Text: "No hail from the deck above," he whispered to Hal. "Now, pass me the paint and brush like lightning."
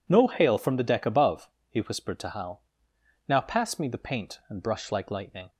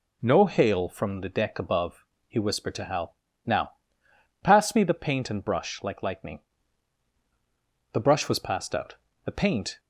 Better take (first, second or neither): first